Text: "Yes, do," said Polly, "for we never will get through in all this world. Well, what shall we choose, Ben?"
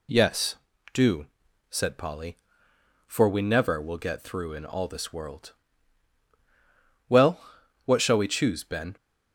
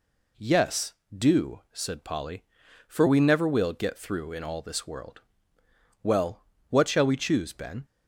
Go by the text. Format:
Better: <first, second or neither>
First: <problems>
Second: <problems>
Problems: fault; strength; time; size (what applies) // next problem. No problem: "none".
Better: neither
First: none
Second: none